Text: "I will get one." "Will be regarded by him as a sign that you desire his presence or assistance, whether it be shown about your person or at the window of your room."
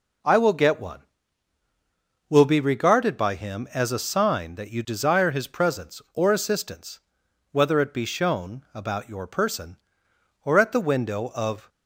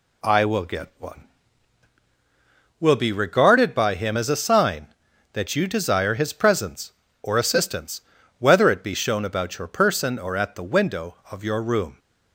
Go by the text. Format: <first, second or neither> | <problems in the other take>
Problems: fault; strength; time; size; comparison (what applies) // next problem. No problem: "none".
second | stops before "your room"; at 11.6 s